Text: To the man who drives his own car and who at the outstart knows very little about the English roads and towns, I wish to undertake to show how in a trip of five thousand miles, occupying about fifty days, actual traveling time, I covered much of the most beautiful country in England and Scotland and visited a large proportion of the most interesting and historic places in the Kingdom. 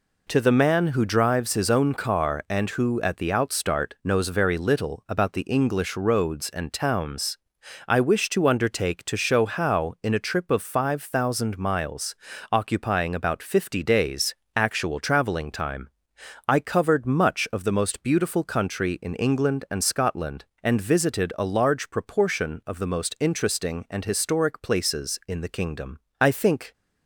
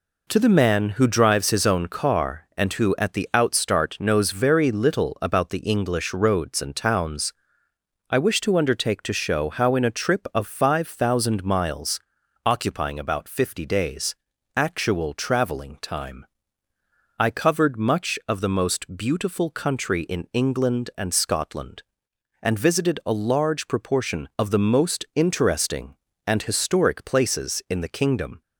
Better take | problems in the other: second | goes on to say "I think"; from 26.1 s on; 0.54 s long

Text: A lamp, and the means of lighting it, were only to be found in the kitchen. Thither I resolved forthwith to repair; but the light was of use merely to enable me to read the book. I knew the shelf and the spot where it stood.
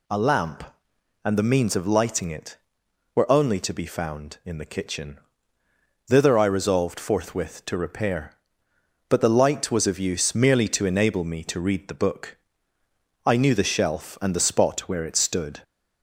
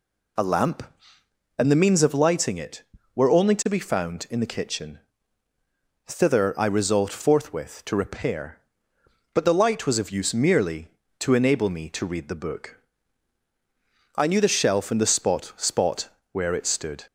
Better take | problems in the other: first | says "spot" twice; at 15.5 s

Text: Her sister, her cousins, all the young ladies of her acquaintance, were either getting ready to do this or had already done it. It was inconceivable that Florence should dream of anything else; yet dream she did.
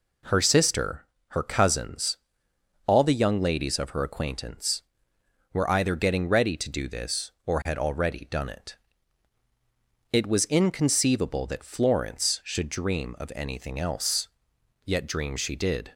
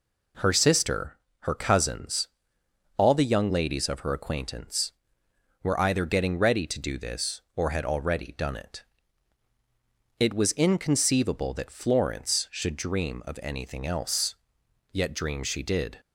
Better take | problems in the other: neither | none

